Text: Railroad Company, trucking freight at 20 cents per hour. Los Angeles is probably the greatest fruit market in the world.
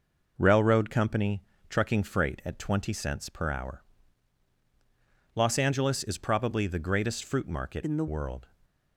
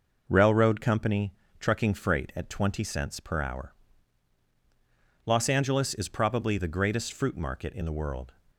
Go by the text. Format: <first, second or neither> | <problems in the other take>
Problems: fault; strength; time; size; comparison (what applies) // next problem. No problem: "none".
second | changes voice from "in" to "the"; from 7.8 to 8.0 s; 0.2 s long